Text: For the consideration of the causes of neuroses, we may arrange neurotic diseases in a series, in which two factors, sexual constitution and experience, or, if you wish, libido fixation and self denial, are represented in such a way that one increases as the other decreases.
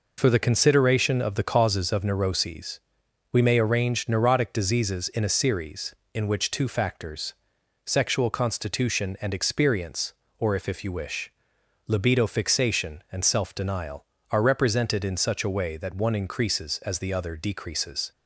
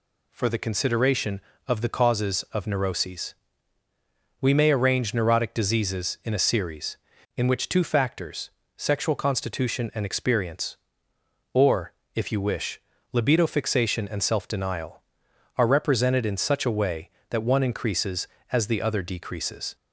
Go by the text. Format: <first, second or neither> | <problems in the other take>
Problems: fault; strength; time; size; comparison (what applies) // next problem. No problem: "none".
second | says "if" twice; at 10.6 s